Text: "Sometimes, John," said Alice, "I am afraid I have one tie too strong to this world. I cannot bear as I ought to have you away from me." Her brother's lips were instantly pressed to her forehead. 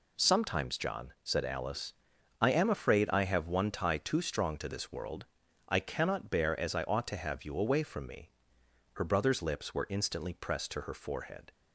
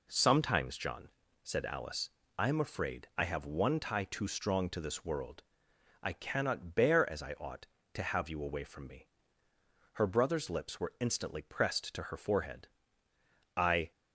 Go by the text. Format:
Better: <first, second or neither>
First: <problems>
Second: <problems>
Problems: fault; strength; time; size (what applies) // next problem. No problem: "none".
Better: first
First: none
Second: goes on to say "I"; slight; from 13.5 s on; 0.34 s long